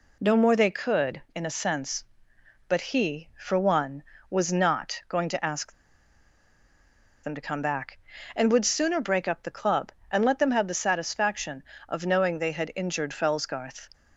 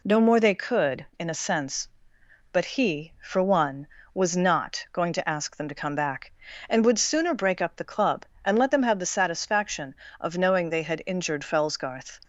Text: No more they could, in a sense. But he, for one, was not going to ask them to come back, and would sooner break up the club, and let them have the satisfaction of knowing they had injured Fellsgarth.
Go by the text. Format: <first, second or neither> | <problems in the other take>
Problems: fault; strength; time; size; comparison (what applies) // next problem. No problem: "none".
second | pauses between "ask" and "them"; strong; at 5.7 s; 1.5 s long